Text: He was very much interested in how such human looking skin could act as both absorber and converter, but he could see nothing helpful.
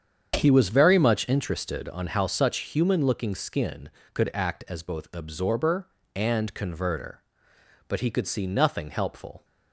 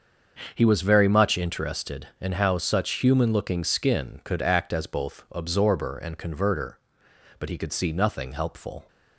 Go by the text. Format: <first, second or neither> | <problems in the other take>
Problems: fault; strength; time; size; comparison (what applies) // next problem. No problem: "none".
second | starts louder than the rest; strong; until 1.3 s; 7.5 dB; also in the second // says "on" for "in"; at 1.8 s